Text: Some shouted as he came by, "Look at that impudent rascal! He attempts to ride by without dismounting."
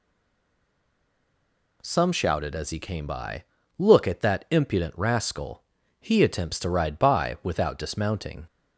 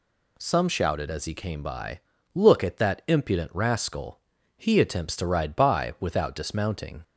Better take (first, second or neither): second